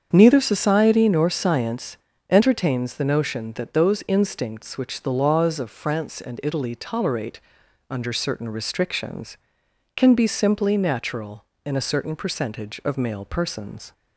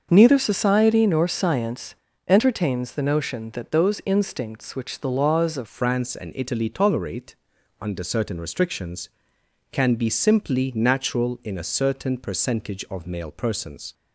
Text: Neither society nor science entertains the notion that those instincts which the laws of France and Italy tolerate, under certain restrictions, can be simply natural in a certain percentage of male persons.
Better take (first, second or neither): first